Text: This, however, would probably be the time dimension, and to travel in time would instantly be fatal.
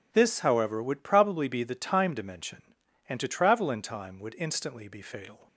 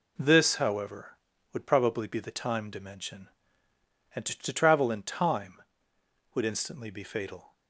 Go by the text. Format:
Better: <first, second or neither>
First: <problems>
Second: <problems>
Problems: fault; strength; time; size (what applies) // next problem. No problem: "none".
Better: first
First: none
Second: says "to" twice; at 4.3 s